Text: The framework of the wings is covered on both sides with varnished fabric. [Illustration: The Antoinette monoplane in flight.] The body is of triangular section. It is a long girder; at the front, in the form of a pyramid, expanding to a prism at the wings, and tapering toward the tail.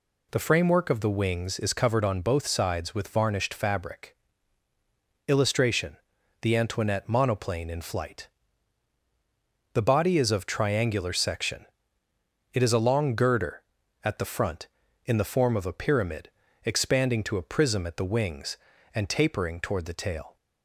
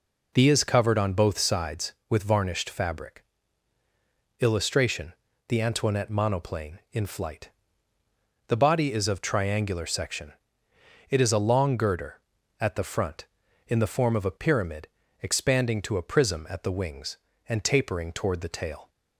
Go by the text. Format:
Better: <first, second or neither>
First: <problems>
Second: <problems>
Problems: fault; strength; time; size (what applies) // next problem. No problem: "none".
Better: first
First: none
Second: skips "framework of the wings"; at 0.4 s